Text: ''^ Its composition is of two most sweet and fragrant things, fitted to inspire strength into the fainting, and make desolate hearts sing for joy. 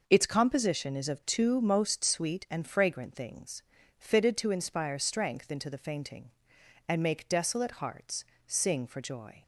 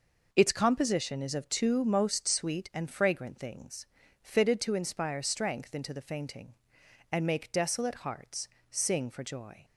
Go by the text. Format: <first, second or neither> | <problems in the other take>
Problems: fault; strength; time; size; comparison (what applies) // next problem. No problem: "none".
neither | pauses between "hearts" and "sing"; slight; the same in both